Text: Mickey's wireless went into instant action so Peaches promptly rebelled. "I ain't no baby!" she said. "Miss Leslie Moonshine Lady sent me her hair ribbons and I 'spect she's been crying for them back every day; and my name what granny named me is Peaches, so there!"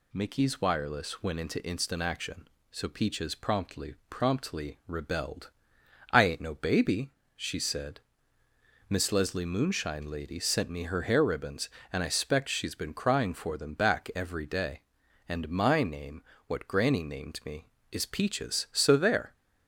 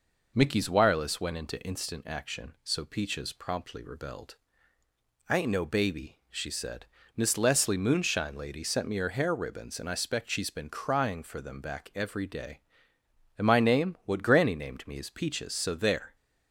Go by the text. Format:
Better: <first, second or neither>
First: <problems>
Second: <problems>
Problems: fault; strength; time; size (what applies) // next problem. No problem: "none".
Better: second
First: says "promptly" twice; at 4.0 s // pauses between "name" and "what"; slight; at 16.2 s; 0.24 s long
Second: none